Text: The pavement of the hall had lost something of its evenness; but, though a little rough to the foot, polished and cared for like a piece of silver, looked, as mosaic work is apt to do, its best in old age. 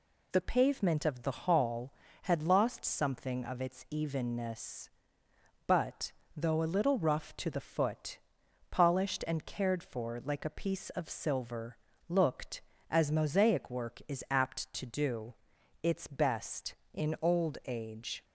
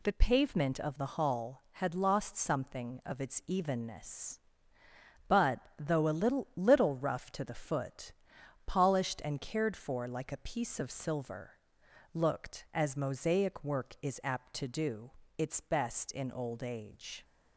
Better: first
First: none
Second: says "little" twice; at 6.5 s

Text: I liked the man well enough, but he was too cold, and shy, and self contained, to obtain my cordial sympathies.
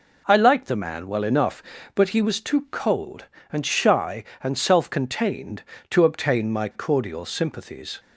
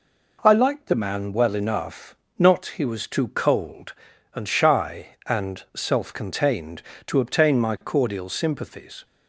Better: first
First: none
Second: says "not" for "but"; at 2.3 s

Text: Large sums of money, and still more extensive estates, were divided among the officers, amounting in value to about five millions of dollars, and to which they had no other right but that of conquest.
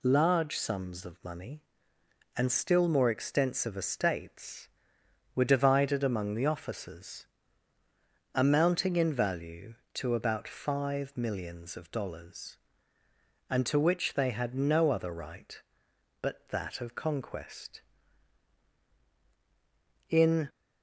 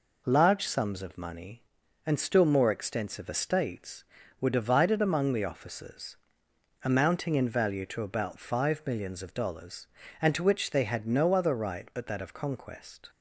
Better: second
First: goes on to say "In"; slight; from 20.0 s on; 0.40 s long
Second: none

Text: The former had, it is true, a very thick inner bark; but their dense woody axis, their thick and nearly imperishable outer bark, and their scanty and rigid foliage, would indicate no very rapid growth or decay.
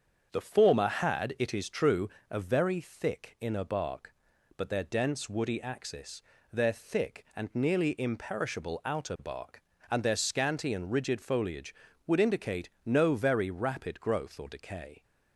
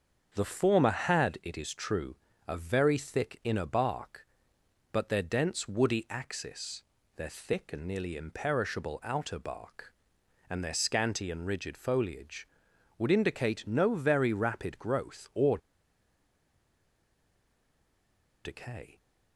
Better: first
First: starts louder than the rest; until 1.3 s; 7 dB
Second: starts louder than the rest; until 1.3 s; 6.5 dB // pauses between "or" and "decay"; strong; at 15.5 s; 2.8 s long

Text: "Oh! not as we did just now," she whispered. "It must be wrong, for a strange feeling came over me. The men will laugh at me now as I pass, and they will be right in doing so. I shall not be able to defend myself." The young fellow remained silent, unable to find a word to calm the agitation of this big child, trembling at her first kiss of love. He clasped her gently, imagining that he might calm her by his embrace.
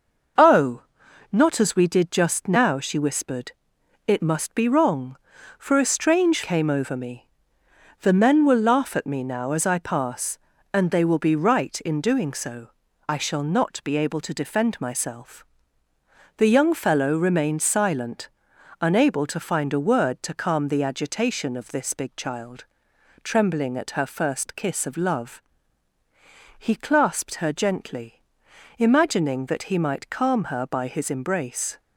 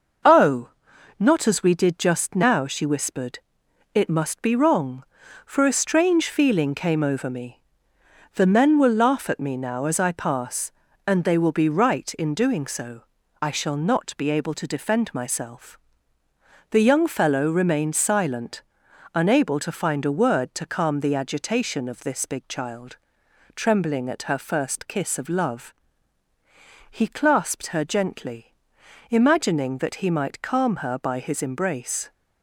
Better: second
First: skips "feeling"; at 6.4 s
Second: none

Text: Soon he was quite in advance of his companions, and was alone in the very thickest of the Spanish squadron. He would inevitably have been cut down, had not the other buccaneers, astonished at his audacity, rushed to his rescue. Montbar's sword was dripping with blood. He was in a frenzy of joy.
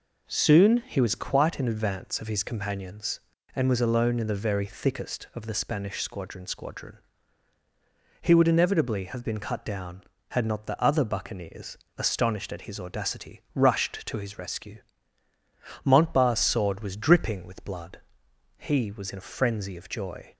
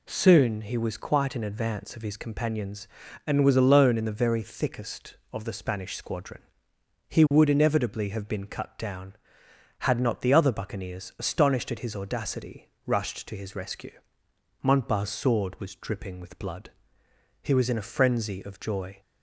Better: second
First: says "squadron" twice; at 6.4 s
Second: none

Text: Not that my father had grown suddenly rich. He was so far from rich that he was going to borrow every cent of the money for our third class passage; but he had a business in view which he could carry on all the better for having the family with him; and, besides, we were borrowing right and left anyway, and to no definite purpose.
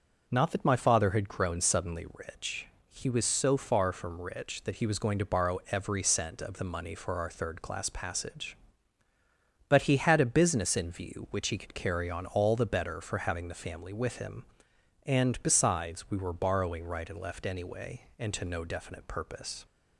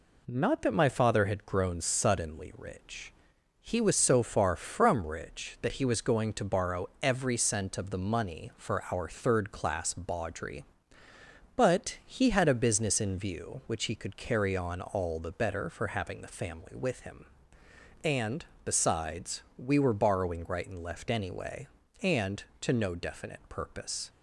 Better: first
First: none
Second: pauses between "borrow" and "every"; slight; at 6.8 s; 0.16 s long // says "bawdry" for "passage"; at 9.9 s

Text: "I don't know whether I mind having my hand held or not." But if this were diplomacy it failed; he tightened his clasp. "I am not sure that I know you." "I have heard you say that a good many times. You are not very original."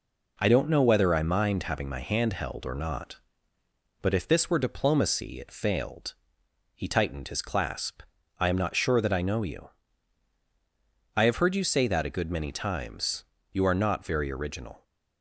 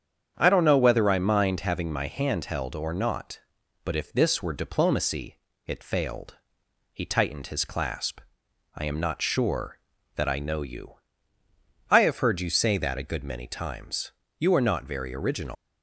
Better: first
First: none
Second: starts louder than the rest; strong; until 1.3 s; 8 dB // pauses between "diplomacy" and "it"; slight; at 5.3 s; 0.28 s long // leaves "original" unfinished; at 15.5 s; 135 ms

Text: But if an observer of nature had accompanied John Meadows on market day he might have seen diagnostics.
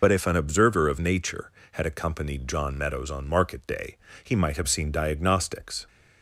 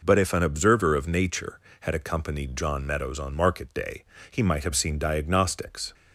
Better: second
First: loses the start of "But"; at 0.0 s; 75 ms // pauses between "day" and "he"; slight; at 3.9 s; 0.28 s long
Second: pauses between "day" and "he"; slight; at 4.0 s; 0.28 s long

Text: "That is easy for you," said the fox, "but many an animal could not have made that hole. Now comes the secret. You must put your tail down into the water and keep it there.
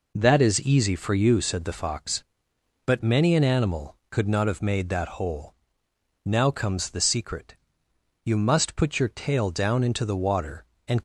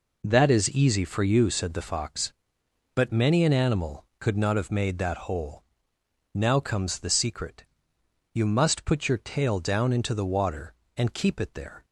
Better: second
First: stops before "keep it there"; at 10.9 s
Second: none

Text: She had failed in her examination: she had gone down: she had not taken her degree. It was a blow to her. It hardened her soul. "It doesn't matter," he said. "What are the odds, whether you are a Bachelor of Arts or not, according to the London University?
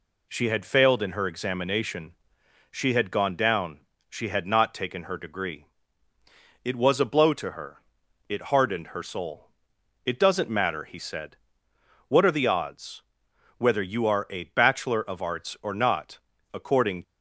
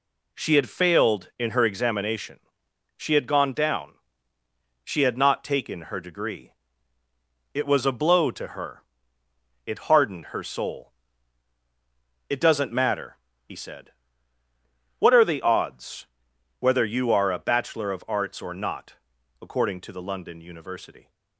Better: second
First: stops before "to the London University"; at 17.0 s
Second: none

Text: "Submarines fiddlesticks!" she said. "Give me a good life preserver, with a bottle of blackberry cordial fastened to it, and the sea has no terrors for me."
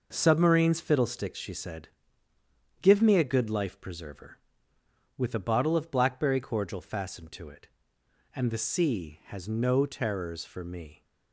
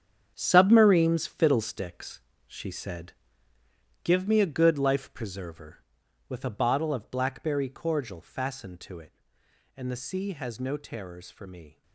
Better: first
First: none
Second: gets quieter; strong; throughout; 12 dB

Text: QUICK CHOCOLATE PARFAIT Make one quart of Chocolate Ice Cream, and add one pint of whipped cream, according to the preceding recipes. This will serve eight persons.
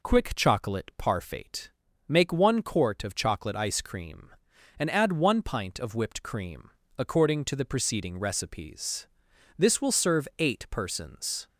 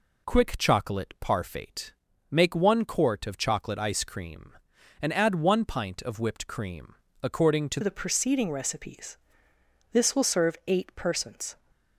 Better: first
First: pauses between "PARFAIT" and "Make"; at 1.6 s; 0.38 s long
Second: pauses between "PARFAIT" and "Make"; at 1.9 s; 0.38 s long // changes voice at "the"; from 7.8 s on; 3.7 s long

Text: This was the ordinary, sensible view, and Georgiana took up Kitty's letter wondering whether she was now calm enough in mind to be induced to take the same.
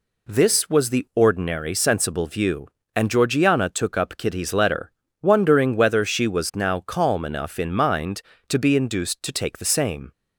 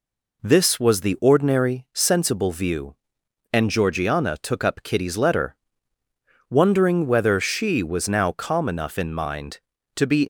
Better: first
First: pauses between "letter" and "wondering"; slight; at 4.9 s; 0.28 s long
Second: pauses between "letter" and "wondering"; noticeable; at 5.5 s; 0.96 s long // stops before "induced to take the same"; at 10.2 s

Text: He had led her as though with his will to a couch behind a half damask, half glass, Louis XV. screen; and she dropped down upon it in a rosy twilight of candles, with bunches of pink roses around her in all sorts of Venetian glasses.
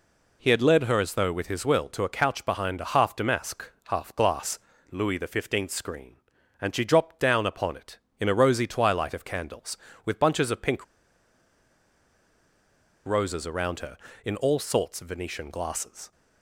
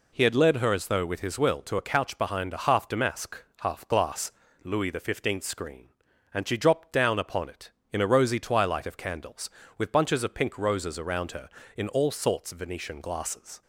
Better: second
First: pauses between "pink" and "roses"; strong; at 10.8 s; 2.2 s long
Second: none

